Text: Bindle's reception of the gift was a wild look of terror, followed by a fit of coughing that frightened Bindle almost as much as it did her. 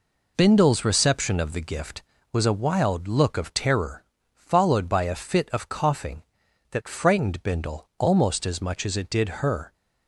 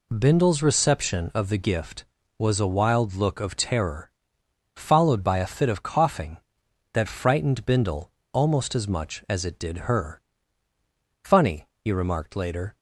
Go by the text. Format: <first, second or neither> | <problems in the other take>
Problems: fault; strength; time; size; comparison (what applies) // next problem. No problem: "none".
first | pauses between "Bindle" and "almost"; slight; at 8.0 s; 0.22 s long // goes on to say "Funny he remarked later"; from 11.2 s on; 1.5 s long